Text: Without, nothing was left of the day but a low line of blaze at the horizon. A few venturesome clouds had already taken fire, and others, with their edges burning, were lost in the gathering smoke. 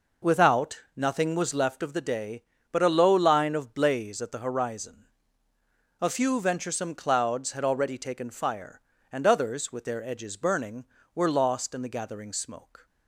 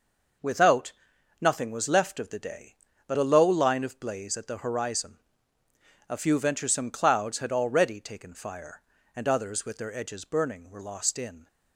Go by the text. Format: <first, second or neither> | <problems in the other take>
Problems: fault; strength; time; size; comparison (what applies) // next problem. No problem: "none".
first | stops before "the gathering smoke"; at 11.4 s